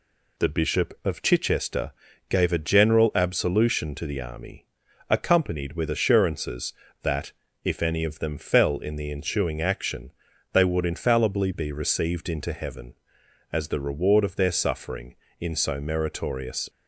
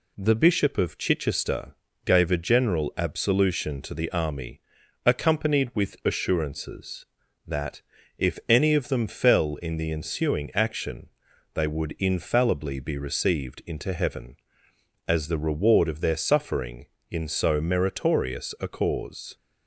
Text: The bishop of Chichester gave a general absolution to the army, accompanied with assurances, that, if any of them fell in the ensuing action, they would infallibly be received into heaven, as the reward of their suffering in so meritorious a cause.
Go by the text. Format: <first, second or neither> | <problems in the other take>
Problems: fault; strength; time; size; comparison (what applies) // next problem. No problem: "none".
second | pauses between "Chichester" and "gave"; slight; at 1.9 s; 0.36 s long; slight in the second // stops before "a cause"; at 16.6 s